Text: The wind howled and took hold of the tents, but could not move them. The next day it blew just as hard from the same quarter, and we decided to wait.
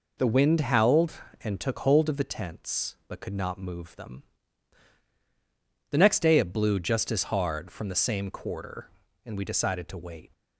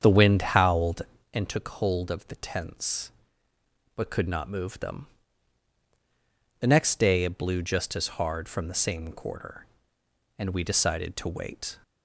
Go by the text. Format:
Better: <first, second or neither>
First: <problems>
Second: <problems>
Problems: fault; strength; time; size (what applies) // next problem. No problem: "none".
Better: first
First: none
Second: starts louder than the rest; strong; until 1.4 s; 7.5 dB